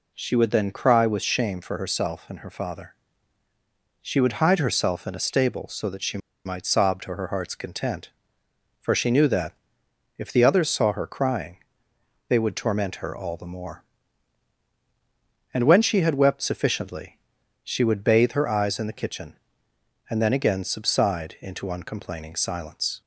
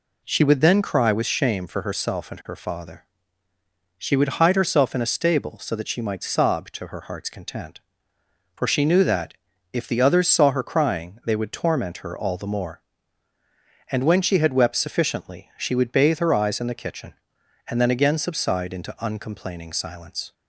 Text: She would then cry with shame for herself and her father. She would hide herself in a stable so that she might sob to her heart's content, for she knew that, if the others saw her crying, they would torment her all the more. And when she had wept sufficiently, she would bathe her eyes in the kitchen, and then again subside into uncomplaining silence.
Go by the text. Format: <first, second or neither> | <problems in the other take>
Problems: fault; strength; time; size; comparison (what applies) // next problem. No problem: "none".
second | pauses between "she" and "might"; slight; at 6.1 s; 0.27 s long